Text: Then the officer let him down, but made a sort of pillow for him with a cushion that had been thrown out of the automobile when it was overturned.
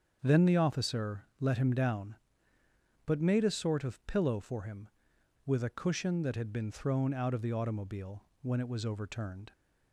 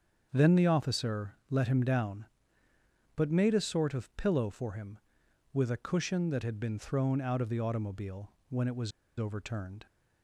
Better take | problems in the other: first | starts louder than the rest; strong; until 1.3 s; 7 dB; strong in the first // pauses between "automobile" and "when"; slight; at 8.3 s; 0.18 s long; slight in the first // pauses between "was" and "overturned"; slight; at 8.9 s; 0.28 s long

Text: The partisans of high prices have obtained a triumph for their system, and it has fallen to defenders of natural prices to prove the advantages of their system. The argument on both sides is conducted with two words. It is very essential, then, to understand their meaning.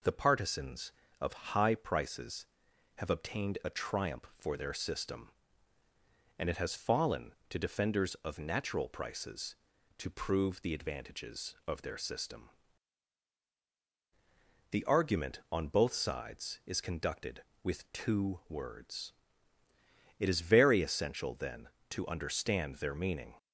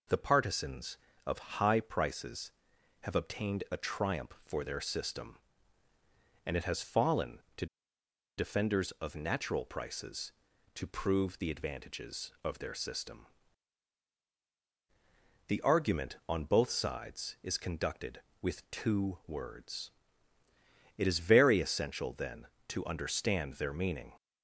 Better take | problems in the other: first | pauses between "to" and "defenders"; noticeable; at 7.6 s; 0.72 s long

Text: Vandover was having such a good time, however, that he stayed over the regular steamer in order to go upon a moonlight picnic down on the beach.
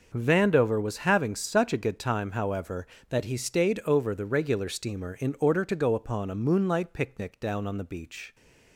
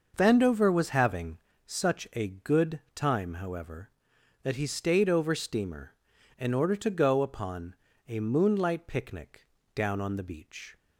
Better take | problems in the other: first | starts louder than the rest; noticeable; until 1.1 s; 6 dB; also in the first // pauses between "having" and "such"; slight; at 1.3 s; 0.26 s long // pauses between "good" and "time"; slight; at 2.7 s; 0.16 s long // skips "the regular"; at 5.3 s // pauses between "upon" and "a"; slight; at 7.7 s; 0.32 s long // pauses between "picnic" and "down"; slight; at 9.4 s; 0.28 s long

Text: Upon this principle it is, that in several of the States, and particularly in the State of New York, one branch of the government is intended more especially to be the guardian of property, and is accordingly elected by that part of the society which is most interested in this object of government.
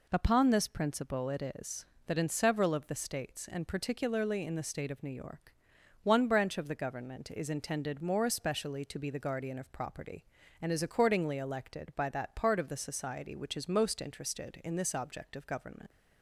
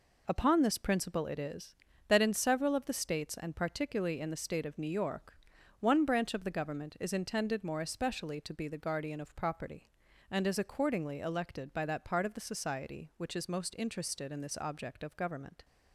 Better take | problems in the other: neither | none

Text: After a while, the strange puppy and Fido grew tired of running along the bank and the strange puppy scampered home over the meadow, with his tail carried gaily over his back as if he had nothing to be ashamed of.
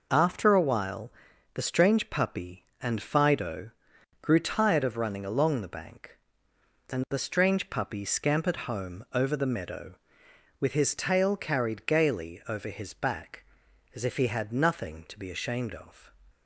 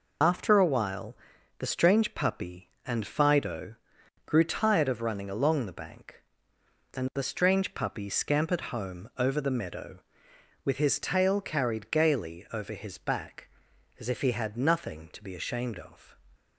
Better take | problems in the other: first | loses the start of "After"; at 0.2 s; 60 ms // pauses between "Fido" and "grew"; noticeable; at 3.7 s; 0.50 s long; noticeable in the first

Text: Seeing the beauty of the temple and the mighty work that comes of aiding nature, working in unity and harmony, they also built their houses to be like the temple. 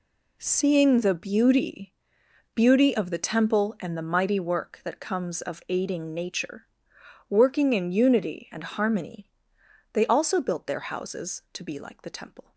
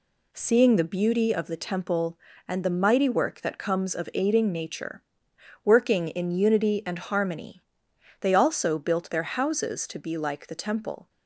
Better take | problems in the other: second | says "beauty" twice; at 2.5 s

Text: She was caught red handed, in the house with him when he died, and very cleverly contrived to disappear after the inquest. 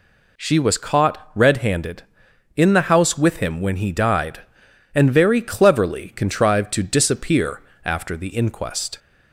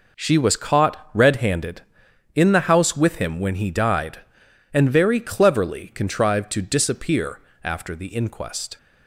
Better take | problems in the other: first | gets quieter; strong; throughout; 8.5 dB // pauses between "disappear" and "after"; slight; at 7.4 s; 0.22 s long; slight in the first

